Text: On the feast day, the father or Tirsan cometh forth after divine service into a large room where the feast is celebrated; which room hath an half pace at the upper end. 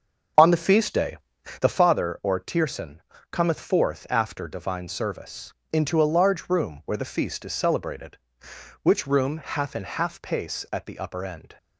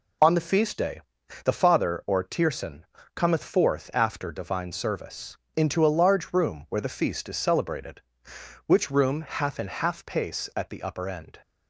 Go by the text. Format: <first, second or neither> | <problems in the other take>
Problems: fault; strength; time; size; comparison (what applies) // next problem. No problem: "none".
second | starts louder than the rest; strong; until 1.9 s; 7 dB // pauses between "Tirsan" and "cometh"; slight; at 3.0 s; 0.30 s long; slight in the second // pauses between "service" and "into"; slight; at 5.5 s; 0.18 s long; slight in the second